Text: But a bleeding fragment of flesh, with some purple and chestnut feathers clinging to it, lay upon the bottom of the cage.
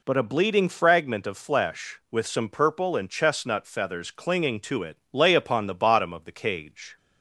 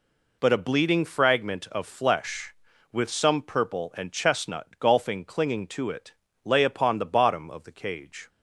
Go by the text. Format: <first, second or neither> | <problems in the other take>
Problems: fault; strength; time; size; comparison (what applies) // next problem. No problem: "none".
first | says "golfing" for "feathers"; at 4.7 s